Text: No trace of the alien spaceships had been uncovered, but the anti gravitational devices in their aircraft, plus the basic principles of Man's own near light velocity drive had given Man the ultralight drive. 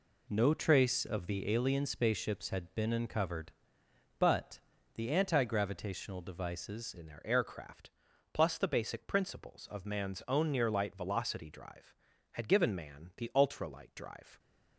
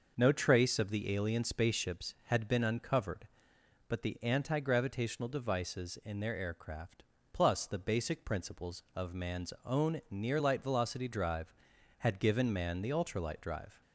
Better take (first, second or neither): second